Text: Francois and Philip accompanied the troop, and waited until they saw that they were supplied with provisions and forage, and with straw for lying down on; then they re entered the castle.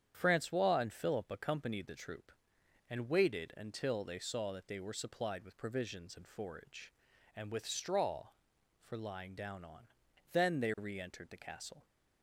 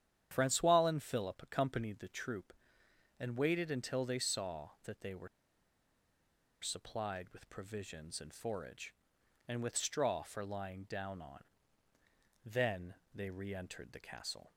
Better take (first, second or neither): first